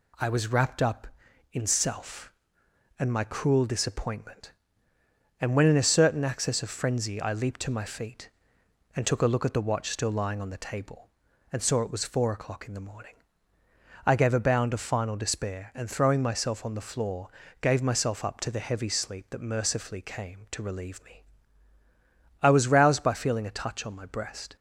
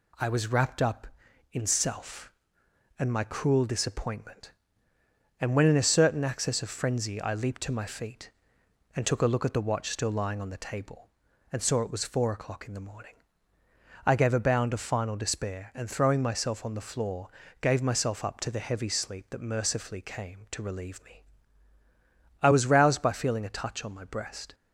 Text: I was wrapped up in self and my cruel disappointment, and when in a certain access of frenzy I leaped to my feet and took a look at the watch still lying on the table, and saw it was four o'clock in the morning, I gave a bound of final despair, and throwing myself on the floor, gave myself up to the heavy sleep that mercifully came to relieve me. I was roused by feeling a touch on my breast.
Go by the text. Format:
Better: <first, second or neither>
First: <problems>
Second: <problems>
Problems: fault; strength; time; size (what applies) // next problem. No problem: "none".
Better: neither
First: none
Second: none